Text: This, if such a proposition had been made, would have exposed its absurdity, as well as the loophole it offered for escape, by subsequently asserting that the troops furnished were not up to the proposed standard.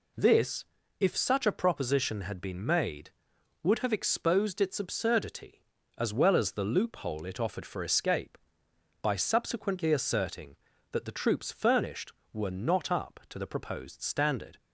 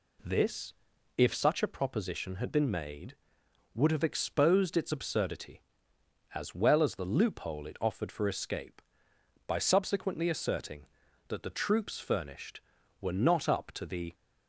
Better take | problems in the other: first | stops before "proposed standard"; at 14.1 s

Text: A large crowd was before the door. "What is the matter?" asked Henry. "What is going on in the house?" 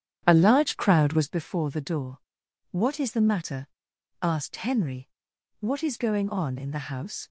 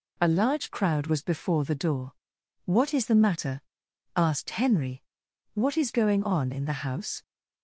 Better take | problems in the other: second | starts louder than the rest; strong; until 1.4 s; 10 dB

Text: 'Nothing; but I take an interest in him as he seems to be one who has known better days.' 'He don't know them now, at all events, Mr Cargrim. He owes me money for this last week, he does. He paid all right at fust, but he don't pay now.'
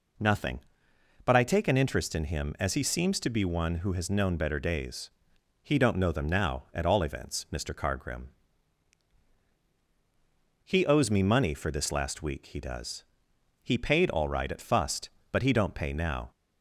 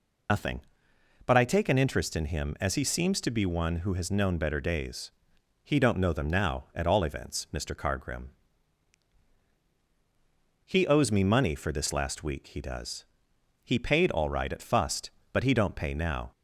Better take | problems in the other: first | loses the start of "Nothing"; at 0.2 s; 115 ms

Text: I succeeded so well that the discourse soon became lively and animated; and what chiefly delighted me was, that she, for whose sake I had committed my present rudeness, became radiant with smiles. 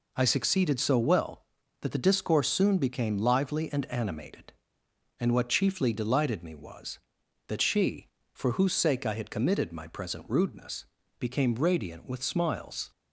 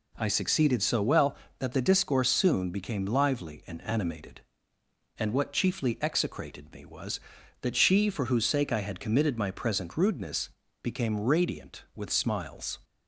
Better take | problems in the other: first | says "execrated" for "delighted"; at 6.0 s

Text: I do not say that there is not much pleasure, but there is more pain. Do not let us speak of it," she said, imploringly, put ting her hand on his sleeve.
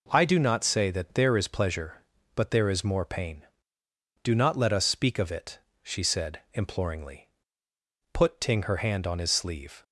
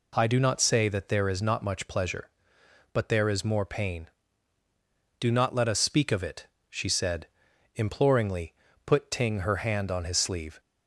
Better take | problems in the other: second | skips "not much"; at 1.4 s

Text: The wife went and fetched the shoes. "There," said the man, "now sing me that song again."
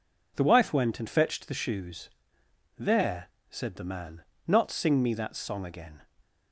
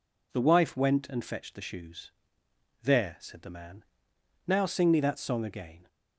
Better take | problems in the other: second | says "not" for "now"; at 4.4 s

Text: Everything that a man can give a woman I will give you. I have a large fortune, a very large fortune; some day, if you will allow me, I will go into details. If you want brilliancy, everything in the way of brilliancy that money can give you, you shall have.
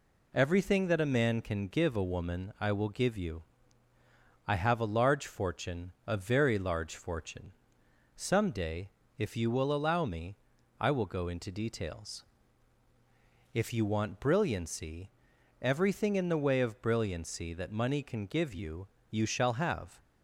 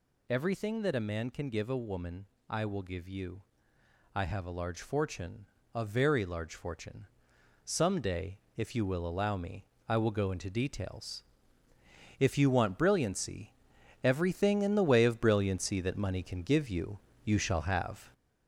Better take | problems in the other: first | gets louder; noticeable; throughout; 5 dB // pauses between "woman" and "I"; slight; at 2.2 s; 0.22 s long

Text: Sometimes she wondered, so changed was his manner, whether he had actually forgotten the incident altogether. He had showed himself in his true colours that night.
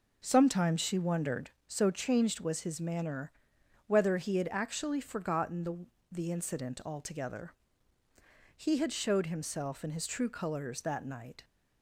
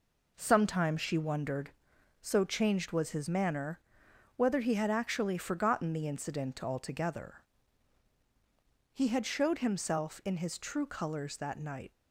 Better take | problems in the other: second | says "the" twice; at 6.1 s

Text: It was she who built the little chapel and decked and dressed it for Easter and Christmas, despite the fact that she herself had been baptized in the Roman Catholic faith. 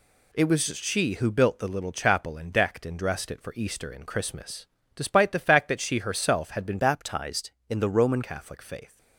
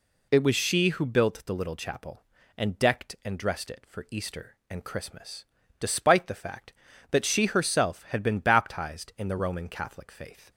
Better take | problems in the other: second | changes voice from "baptized" to "Roman"; from 6.7 to 8.2 s; 1.5 s long

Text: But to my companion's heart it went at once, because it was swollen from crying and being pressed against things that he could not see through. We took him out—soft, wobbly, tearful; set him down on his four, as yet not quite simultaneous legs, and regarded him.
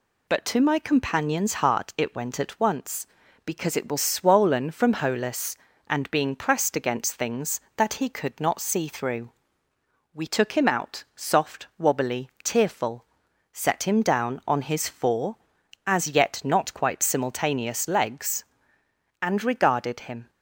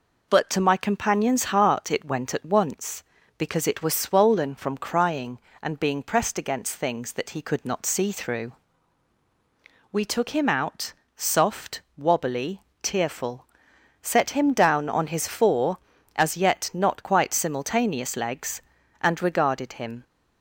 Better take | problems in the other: second | says "holus" for "crying"; at 4.9 s

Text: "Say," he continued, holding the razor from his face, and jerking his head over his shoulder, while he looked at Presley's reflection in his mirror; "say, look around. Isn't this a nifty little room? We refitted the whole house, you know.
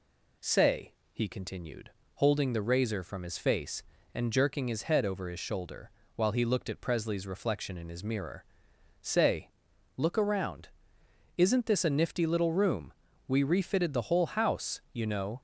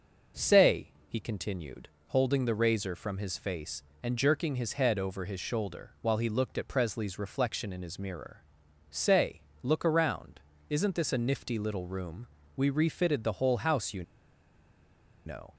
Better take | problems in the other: first | pauses between "you" and "know"; at 14.0 s; 1.2 s long

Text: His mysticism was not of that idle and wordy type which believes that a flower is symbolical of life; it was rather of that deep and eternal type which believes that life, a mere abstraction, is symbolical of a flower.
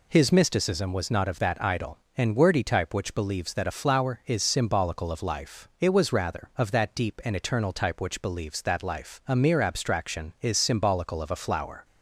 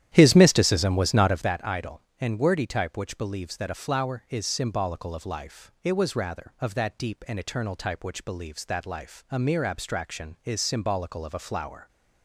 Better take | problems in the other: first | starts louder than the rest; strong; until 1.6 s; 11.5 dB

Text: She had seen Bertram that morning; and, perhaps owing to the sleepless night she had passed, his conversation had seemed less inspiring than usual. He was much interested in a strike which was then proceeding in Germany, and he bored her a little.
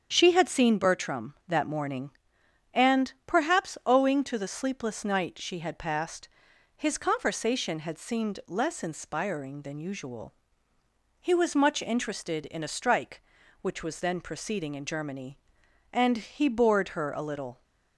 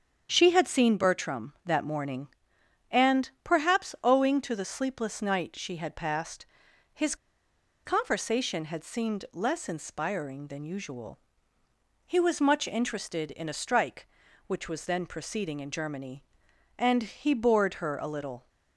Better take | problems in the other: first | starts louder than the rest; strong; until 1.3 s; 7.5 dB; strong in the first // pauses between "his" and "conversation"; noticeable; at 7.1 s; 0.69 s long

